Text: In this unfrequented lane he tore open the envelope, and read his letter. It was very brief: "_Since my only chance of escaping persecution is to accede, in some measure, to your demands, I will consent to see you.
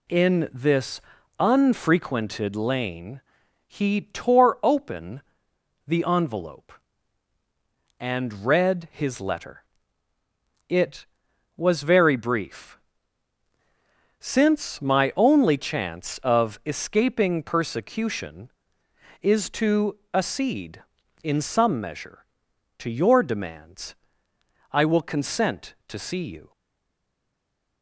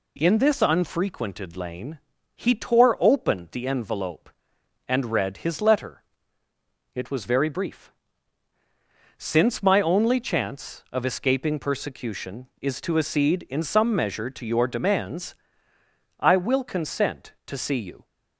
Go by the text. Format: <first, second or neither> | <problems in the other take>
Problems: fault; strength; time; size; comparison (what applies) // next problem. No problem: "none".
second | pauses between "this" and "unfrequented"; slight; at 1.0 s; 0.36 s long // pauses between "lane" and "he"; noticeable; at 3.1 s; 0.46 s long; slight in the second // pauses between "open" and "the"; noticeable; at 5.2 s; 0.64 s long // pauses between "to" and "accede"; slight; at 19.9 s; 0.16 s long // stays silent after the last word; noticeable; from 26.5 s on; 1.3 s long